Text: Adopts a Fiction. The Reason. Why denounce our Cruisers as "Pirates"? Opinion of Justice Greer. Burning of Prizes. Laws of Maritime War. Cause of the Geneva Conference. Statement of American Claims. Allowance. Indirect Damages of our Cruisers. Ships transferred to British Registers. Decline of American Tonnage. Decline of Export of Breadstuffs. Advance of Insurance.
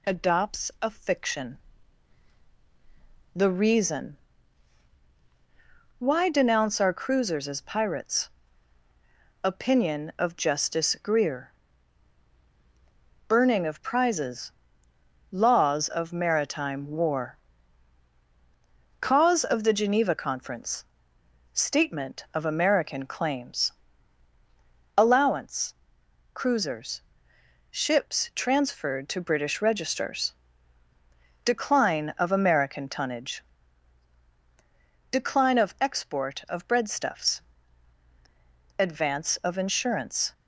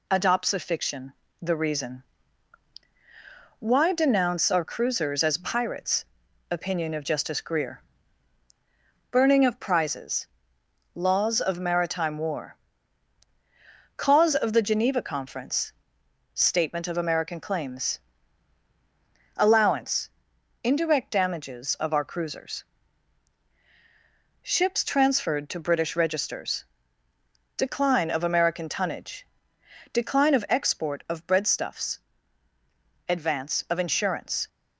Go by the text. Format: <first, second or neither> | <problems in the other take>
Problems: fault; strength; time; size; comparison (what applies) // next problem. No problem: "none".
second | skips "Indirect Damages of our"; at 26.0 s